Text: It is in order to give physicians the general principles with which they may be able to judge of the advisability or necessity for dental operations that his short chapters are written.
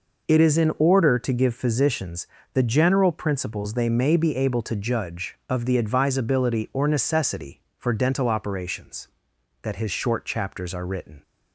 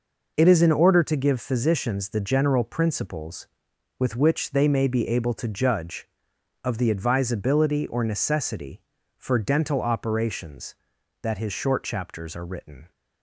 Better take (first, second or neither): second